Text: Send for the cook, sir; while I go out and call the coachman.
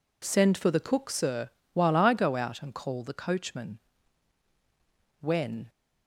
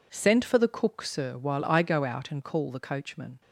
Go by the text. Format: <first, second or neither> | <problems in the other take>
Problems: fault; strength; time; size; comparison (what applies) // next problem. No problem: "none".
second | goes on to say "When"; from 5.1 s on; 0.50 s long